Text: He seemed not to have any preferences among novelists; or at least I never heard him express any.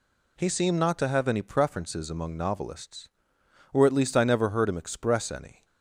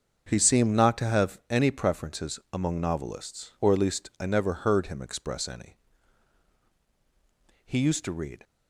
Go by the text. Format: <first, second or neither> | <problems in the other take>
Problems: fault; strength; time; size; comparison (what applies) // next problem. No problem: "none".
first | starts louder than the rest; until 1.2 s; 6.5 dB // goes on to say "He used to read"; noticeable; from 7.6 s on; 0.78 s long